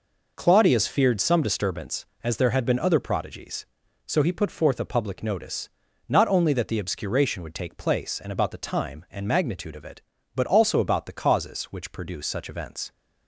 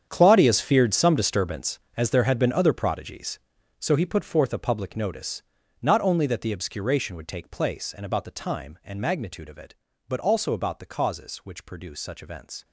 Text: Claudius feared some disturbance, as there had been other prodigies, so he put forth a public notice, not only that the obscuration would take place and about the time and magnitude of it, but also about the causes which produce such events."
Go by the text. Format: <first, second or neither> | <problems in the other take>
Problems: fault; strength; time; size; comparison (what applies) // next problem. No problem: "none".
first | gets quieter; strong; throughout; 15.5 dB